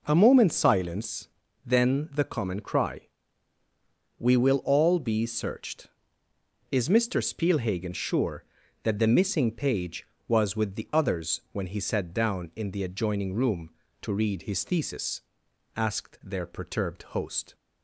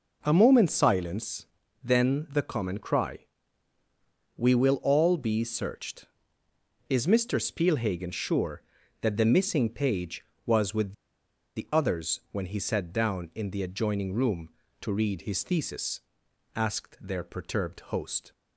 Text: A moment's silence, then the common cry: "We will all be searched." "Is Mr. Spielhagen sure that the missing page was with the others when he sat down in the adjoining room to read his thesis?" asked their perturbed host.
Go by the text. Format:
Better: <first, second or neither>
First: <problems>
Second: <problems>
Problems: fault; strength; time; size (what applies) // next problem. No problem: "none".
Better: first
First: pauses between "perturbed" and "host"; slight; at 17.0 s; 0.16 s long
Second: pauses between "with" and "the"; noticeable; at 10.9 s; 0.63 s long // pauses between "perturbed" and "host"; slight; at 17.7 s; 0.16 s long